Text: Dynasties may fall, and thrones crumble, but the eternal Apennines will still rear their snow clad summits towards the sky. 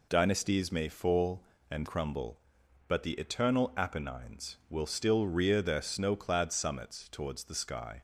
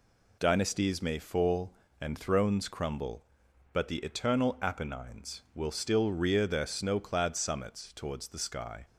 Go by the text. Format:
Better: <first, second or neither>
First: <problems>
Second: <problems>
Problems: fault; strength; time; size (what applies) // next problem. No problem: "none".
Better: second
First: skips "thrones"; at 1.8 s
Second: none